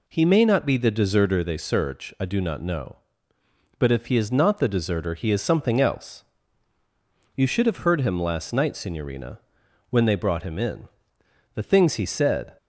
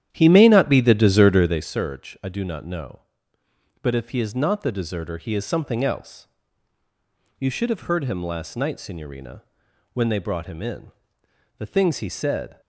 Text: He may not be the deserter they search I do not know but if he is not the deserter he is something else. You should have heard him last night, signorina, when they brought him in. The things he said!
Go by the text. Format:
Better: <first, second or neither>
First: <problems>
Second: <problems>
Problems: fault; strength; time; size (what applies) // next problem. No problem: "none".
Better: first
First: none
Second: starts louder than the rest; strong; until 1.7 s; 11 dB